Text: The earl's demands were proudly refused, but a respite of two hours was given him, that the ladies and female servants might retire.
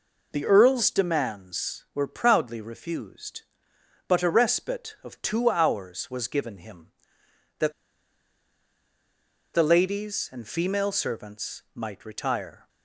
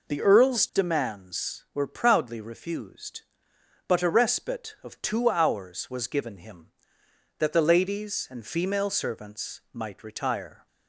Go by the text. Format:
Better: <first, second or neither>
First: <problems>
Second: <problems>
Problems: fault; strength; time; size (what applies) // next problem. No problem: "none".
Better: second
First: pauses between "that" and "the"; strong; at 7.7 s; 1.8 s long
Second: none